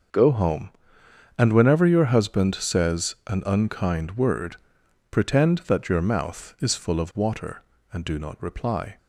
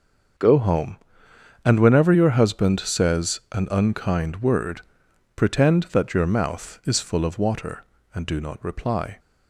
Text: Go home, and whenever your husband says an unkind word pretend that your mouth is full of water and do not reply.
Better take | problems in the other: neither | starts louder than the rest; the same in both // pauses between "word" and "pretend"; noticeable; the same in both

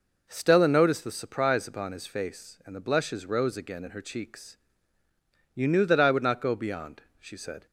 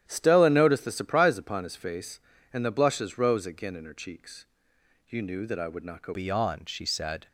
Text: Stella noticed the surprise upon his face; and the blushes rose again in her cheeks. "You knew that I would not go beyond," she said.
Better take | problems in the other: first | starts louder than the rest; strong; until 1.0 s; 11 dB // changes voice at "beyond"; from 6.1 s on; 1.1 s long

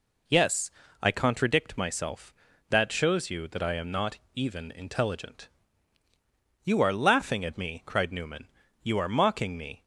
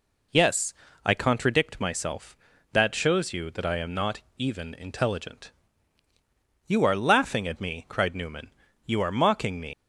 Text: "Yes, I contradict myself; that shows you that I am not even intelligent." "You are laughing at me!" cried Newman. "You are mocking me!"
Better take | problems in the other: first | pauses between "not" and "even"; slight; at 4.2 s; 0.16 s long; slight in the first // leaves "me" unfinished; at 9.7 s; 130 ms

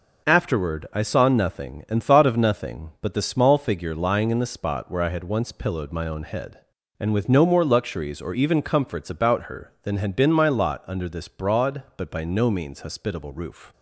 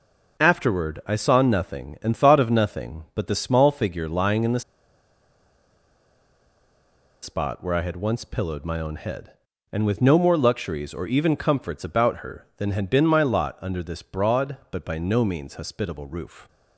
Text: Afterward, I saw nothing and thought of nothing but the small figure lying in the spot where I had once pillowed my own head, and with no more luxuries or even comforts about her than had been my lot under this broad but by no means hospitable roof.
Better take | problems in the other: first | pauses between "the" and "spot"; strong; at 4.6 s; 2.6 s long

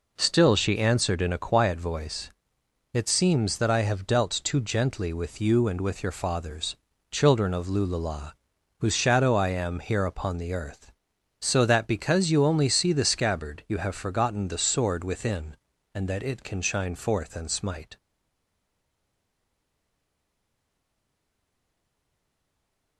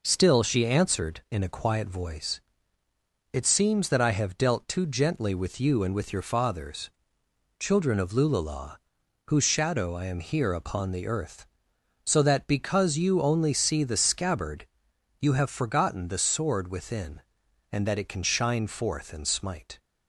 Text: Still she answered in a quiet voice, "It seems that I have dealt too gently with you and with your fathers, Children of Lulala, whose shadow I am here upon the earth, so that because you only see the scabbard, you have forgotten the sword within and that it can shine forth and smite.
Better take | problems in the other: second | stays silent after the last word; strong; from 17.9 s on; 5.0 s long

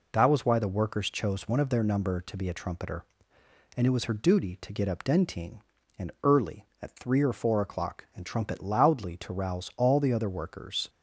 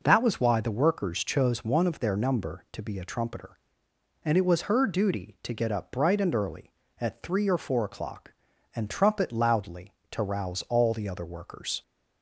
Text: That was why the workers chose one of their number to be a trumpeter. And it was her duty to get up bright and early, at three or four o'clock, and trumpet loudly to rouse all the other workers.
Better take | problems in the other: second | says "dentine" for "bright"; at 5.0 s

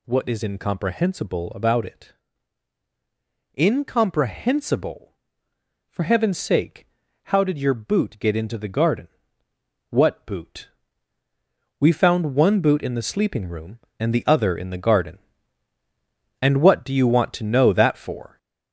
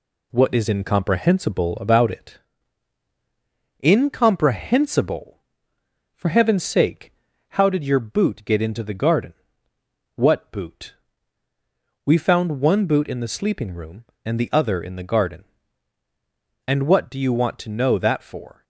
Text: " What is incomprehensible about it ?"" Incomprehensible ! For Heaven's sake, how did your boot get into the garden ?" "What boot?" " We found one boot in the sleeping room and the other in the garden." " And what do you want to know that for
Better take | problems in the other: second | gets louder; slight; throughout; 3 dB

